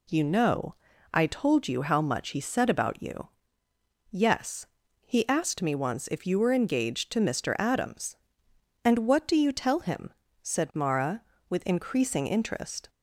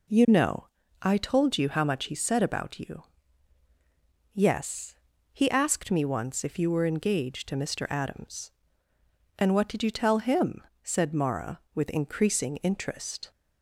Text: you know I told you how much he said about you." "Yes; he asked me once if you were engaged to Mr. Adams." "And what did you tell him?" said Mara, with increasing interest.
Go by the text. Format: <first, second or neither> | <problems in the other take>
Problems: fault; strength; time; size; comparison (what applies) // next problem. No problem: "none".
second | pauses between "know" and "I"; at 0.7 s; 0.38 s long; slight in the second // says "do" for "did"; at 9.2 s